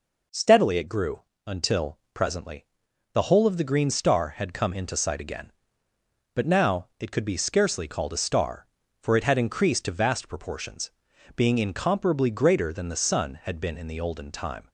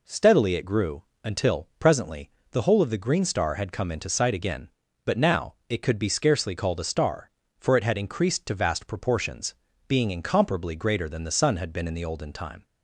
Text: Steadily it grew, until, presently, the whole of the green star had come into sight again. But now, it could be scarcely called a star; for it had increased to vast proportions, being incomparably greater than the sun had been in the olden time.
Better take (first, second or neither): neither